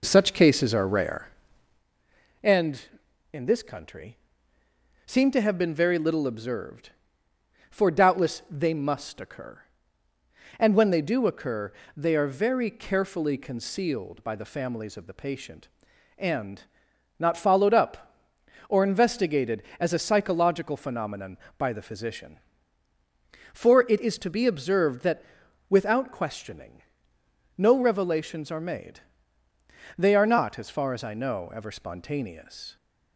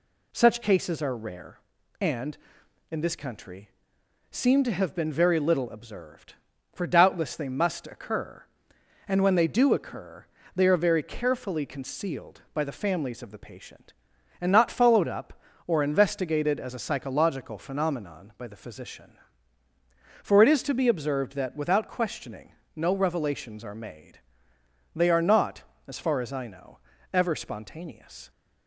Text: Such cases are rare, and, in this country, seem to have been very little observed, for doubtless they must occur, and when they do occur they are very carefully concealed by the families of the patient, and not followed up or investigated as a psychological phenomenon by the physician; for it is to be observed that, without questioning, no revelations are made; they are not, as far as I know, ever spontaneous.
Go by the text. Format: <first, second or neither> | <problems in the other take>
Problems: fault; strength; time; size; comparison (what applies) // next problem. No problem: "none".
second | starts louder than the rest; noticeable; until 1.9 s; 4 dB // pauses between "occur" and "they"; slight; at 11.7 s; 0.24 s long; slight in the second // pauses between "and" and "not"; noticeable; at 16.6 s; 0.54 s long